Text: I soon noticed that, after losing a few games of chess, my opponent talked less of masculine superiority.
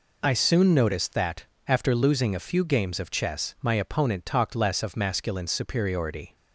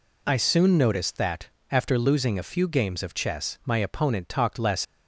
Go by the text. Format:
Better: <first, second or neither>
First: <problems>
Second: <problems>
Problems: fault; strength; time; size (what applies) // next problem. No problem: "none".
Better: first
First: none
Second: stops before "of masculine superiority"; at 4.8 s